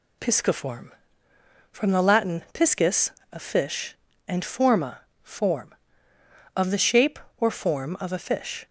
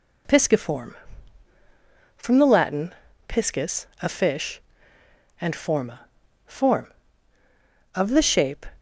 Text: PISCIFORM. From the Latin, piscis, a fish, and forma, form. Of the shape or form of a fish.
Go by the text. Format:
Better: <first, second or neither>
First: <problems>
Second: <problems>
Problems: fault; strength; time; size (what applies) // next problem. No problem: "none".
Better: first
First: none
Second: stops before "or form of a fish"; at 8.7 s